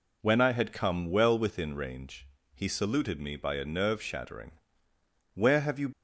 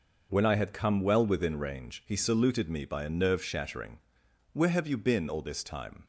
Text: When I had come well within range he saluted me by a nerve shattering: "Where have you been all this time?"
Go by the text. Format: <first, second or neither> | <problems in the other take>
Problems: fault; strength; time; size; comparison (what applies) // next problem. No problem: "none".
second | pauses between "range" and "he"; slight; at 2.2 s; 0.28 s long // stops before "been all this time"; at 5.9 s